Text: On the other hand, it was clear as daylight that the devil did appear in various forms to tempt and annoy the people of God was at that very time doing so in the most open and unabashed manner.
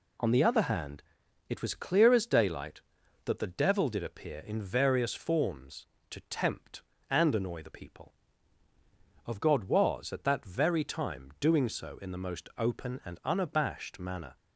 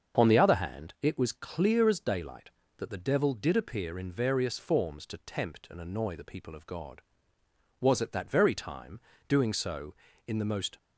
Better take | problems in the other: first | starts louder than the rest; until 1.2 s; 7 dB // pauses between "time" and "doing"; slight; at 8.9 s; 0.28 s long // stops before "open and unabashed manner"; at 10.7 s

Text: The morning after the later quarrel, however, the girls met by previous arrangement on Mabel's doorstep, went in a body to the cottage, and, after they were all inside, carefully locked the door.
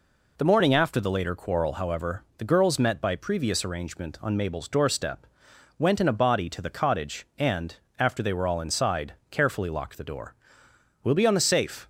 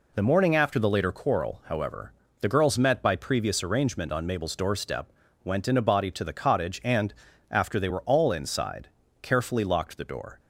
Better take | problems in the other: second | goes on to say "We'll be on the safe"; noticeable; from 11.0 s on; 0.82 s long

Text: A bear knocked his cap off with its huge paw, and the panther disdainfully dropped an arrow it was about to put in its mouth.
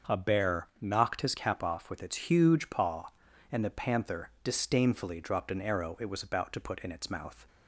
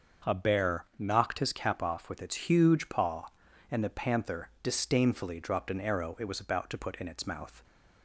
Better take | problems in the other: neither | starts louder than the rest; the same in both

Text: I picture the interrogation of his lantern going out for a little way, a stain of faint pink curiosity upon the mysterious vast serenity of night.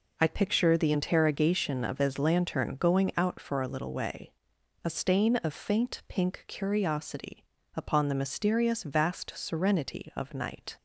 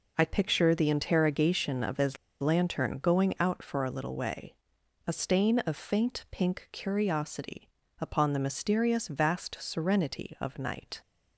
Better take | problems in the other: first | pauses between "his" and "lantern"; slight; at 2.1 s; 0.25 s long // pauses between "curiosity" and "upon"; slight; at 7.6 s; 0.30 s long; slight in the first

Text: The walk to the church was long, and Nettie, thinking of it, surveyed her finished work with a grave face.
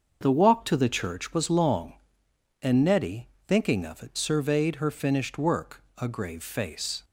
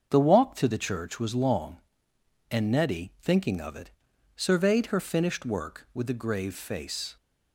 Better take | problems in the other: second | starts louder than the rest; until 1.2 s; 6.5 dB; also in the second // skips "with"; at 5.8 s

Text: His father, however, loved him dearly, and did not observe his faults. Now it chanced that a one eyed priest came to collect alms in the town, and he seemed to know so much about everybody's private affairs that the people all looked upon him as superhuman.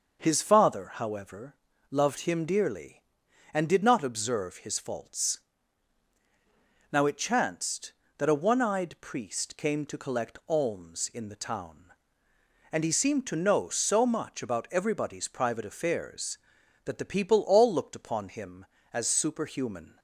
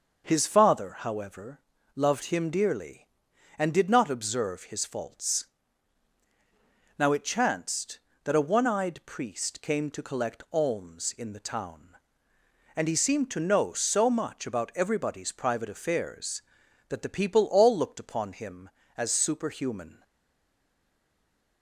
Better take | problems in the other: first | starts louder than the rest; noticeable; until 1.2 s; 6 dB; noticeable in the first // stays silent after the last word; noticeable; from 20.0 s on; 1.6 s long

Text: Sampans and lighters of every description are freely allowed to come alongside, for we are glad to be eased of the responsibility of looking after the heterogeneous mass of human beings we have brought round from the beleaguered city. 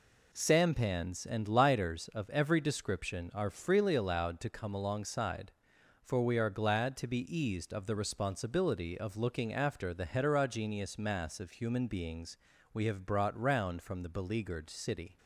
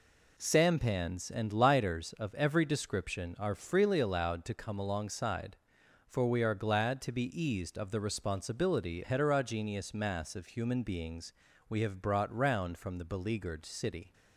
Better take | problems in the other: first | skips "of looking after the"; at 9.0 s // pauses between "beings" and "we"; slight; at 11.3 s; 0.36 s long; slight in the first

